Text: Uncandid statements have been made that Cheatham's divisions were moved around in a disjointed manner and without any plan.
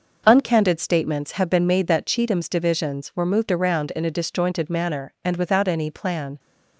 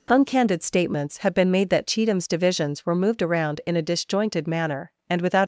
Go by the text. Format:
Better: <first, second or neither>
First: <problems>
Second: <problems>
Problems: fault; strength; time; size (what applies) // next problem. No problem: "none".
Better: first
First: none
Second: stops before "any plan"; at 5.4 s